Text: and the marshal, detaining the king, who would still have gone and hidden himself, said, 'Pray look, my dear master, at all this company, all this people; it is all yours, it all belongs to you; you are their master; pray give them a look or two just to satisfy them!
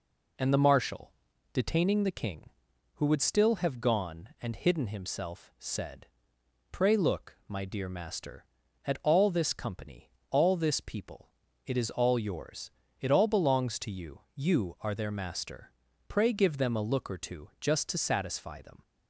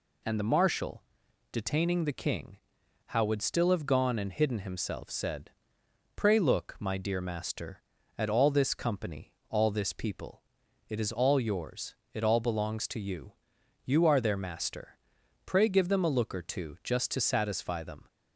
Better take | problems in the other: first | says "how" for "who"; at 3.0 s

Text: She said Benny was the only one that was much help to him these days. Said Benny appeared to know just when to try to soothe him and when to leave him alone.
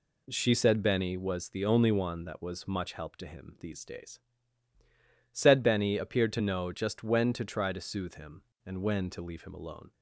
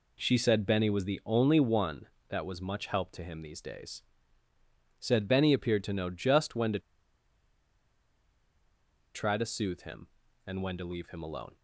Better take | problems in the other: first | pauses between "to" and "try"; strong; at 6.7 s; 2.3 s long

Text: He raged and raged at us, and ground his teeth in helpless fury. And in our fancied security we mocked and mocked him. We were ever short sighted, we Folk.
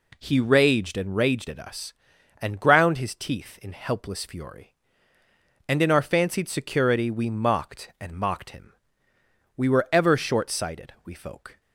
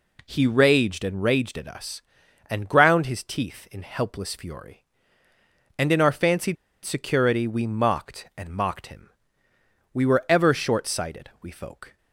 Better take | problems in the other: first | pauses between "fancied" and "security"; slight; at 6.5 s; 0.29 s long

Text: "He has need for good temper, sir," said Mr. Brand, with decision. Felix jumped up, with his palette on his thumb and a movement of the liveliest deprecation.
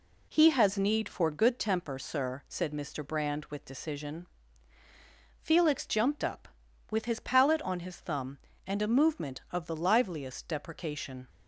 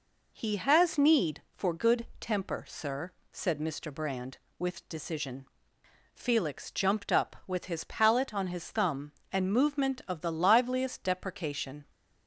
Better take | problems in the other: first | skips "a"; at 9.5 s

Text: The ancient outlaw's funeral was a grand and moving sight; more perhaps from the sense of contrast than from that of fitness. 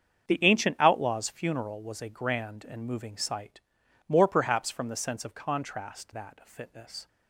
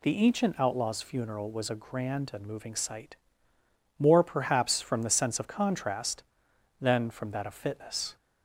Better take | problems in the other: second | starts louder than the rest; strong; until 1.3 s; 7.5 dB // skips "than from"; at 6.1 s

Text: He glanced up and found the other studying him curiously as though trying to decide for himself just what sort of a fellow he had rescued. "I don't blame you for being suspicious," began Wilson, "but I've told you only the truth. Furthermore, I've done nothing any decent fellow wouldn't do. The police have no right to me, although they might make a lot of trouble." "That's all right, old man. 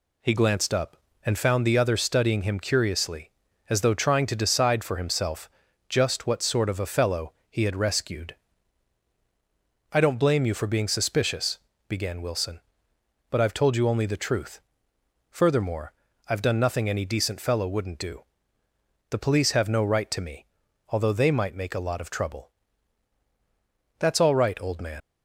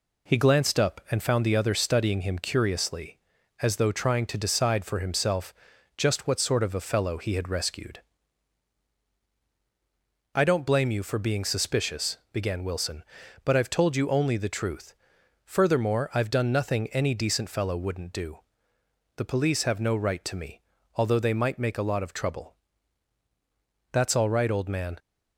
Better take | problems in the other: second | pauses between "himself" and "just"; at 5.4 s; 0.40 s long; also in the second // pauses between "fellow" and "he"; slight; at 7.3 s; 0.18 s long // leaves "man" unfinished; at 25.0 s; 80 ms

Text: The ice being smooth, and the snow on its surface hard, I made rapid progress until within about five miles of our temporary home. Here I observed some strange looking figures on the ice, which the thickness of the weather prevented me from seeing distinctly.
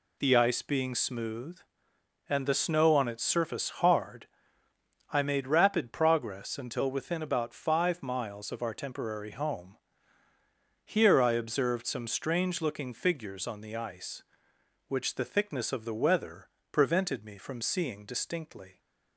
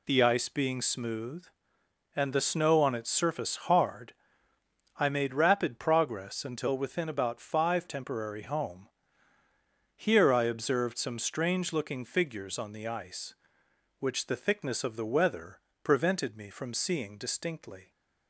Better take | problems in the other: first | skips "miles of our"; at 7.8 s // pauses between "weather" and "prevented"; slight; at 15.5 s; 0.24 s long; slight in the first

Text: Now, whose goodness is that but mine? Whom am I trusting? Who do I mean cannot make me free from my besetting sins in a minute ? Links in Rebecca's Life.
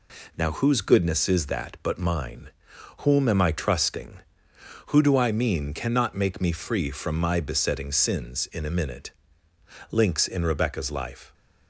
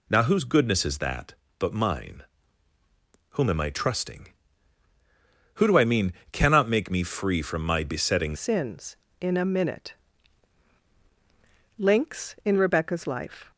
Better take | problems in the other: first | pauses between "mean" and "cannot"; slight; at 6.1 s; 0.18 s long // changes voice at "sins"; from 8.3 s on; 5.2 s long

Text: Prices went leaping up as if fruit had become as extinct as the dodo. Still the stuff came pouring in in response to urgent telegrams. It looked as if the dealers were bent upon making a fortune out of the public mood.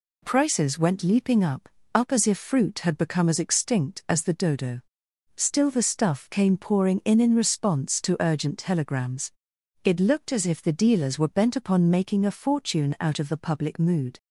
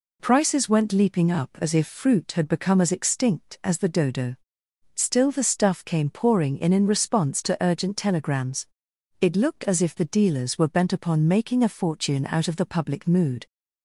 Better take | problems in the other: second | says "up" twice; at 1.9 s

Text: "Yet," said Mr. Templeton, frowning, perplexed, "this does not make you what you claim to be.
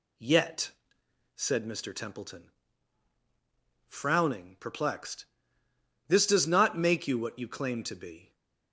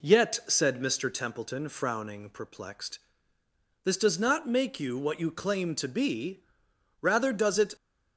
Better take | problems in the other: first | goes on to say "Rather does it"; noticeable; from 7.0 s on; 0.74 s long

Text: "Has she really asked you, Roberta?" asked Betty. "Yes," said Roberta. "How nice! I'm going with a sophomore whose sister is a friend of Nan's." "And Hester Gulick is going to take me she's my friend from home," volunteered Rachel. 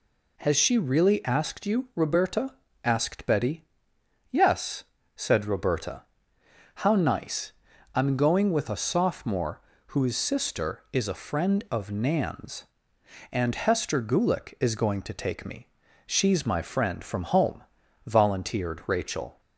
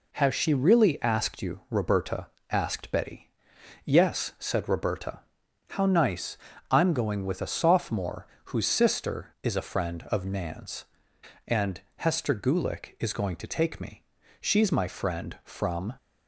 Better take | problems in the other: first | pauses between "sophomore" and "whose"; slight; at 8.2 s; 0.20 s long; slight in the first // pauses between "And" and "Hester"; slight; at 11.8 s; 0.16 s long // pauses between "me" and "she's"; at 14.0 s; 0.38 s long; also in the first // stops before "home volunteered Rachel"; at 15.9 s

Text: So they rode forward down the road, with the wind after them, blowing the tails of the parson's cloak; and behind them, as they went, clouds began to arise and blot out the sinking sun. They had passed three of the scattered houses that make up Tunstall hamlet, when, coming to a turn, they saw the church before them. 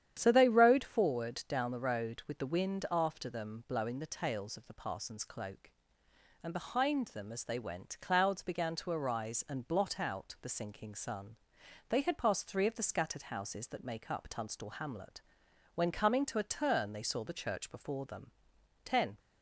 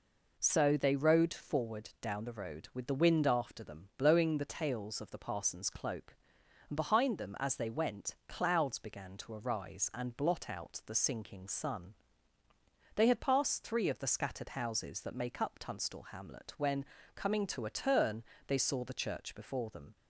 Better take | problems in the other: second | starts louder than the rest; strong; until 1.2 s; 9.5 dB // goes on to say "Ten"; slight; from 18.8 s on; 0.34 s long

